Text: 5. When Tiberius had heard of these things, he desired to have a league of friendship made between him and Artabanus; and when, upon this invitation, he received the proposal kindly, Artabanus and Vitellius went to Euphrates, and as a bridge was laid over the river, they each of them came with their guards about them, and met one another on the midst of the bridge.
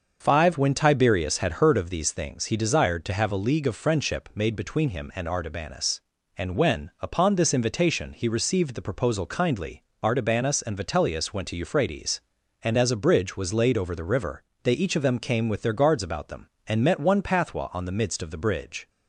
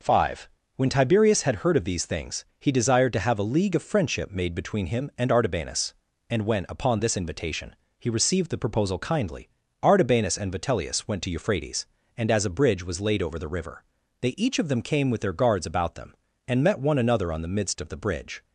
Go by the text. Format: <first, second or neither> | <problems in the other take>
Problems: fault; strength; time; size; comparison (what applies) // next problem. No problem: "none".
second | starts louder than the rest; until 1.2 s; 6.5 dB // says "pathwa" for "another"; at 17.2 s